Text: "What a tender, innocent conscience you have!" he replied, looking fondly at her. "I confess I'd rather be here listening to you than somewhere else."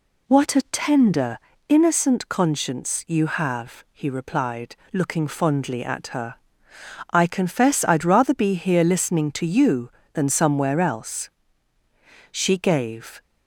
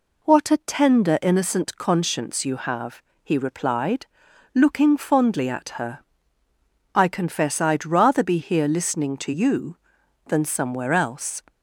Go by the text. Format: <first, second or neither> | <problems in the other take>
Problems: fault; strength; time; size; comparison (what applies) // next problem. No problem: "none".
second | goes on to say "She gave"; noticeable; from 12.3 s on; 0.88 s long